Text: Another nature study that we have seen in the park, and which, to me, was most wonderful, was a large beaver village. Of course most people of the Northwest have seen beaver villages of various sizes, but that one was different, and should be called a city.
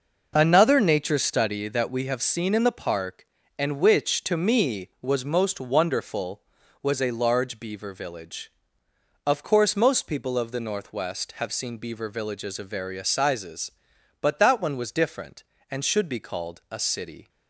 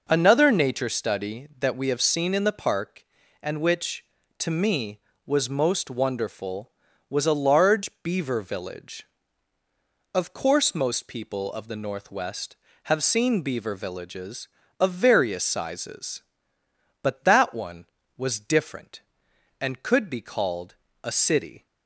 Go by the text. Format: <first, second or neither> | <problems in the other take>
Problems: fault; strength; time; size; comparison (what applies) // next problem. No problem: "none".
first | says "could" for "should"; at 19.8 s // pauses between "called" and "a"; slight; at 20.7 s; 0.28 s long